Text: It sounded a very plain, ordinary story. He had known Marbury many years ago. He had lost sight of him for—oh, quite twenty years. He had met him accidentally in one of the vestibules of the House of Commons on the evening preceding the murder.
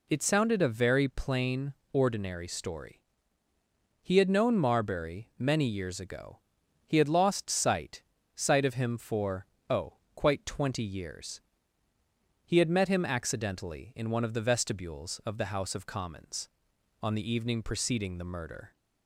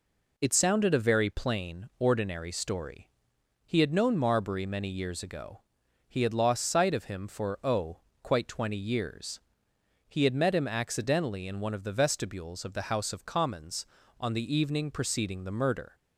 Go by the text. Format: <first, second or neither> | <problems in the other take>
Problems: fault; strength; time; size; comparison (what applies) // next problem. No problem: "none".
second | says "sight" twice; at 8.3 s